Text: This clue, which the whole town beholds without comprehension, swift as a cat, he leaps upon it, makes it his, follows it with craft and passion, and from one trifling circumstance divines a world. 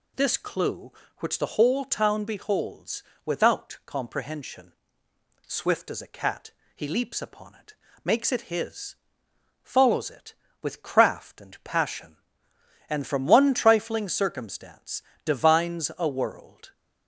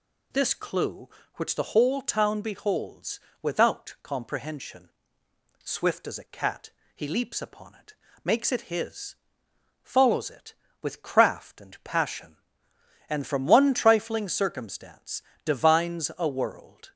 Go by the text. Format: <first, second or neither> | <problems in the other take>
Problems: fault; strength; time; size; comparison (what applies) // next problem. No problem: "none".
neither | pauses between "beholds" and "without"; slight; the same in both // pauses between "circumstance" and "divines"; slight; the same in both